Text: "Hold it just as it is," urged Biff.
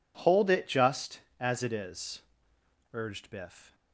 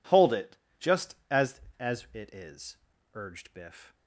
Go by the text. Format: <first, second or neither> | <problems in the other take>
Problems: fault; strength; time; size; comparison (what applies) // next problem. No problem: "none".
first | pauses between "it" and "just"; slight; at 0.5 s; 0.22 s long // says "as" twice; at 1.7 s